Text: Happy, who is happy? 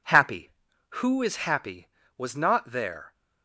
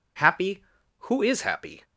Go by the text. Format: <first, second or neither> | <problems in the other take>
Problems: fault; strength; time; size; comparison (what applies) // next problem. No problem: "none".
second | goes on to say "Was not there"; noticeable; from 2.1 s on; 0.96 s long